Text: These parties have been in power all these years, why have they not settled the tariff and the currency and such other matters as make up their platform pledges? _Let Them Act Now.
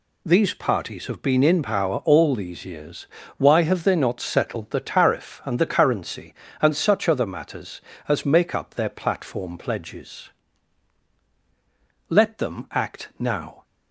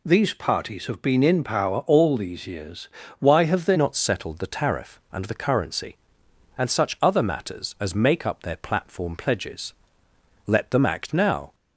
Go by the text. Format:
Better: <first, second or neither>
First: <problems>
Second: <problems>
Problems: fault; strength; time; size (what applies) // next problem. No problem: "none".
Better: first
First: none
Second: changes voice at "not"; from 3.7 s on; 7.8 s long